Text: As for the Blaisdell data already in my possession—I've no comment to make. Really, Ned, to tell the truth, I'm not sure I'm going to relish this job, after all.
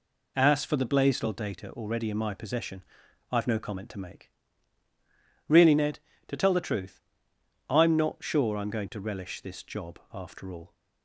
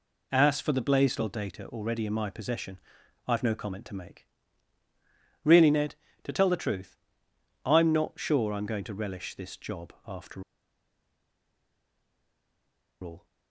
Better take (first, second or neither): first